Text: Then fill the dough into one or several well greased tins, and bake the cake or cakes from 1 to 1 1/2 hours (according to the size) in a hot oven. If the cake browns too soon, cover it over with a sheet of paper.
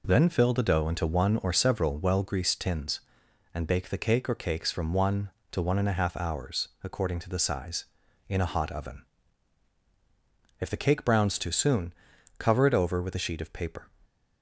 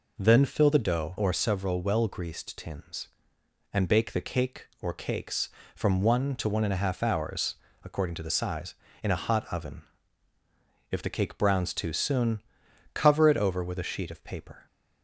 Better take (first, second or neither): first